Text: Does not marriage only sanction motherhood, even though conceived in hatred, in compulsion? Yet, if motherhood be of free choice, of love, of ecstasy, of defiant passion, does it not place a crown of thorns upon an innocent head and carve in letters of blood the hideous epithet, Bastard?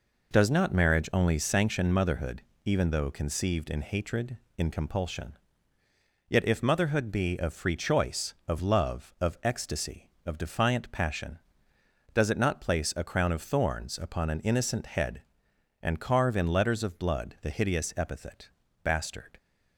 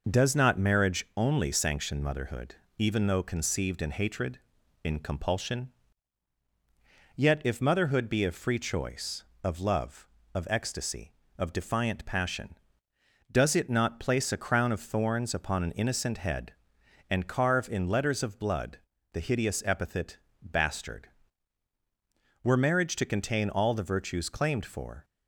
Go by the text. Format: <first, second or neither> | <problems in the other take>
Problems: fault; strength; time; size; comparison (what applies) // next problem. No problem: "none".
first | pauses between "blood" and "the"; slight; at 18.7 s; 0.34 s long // goes on to say "Were marriage to contain all the virtues claimed for"; strong; from 22.4 s on; 2.6 s long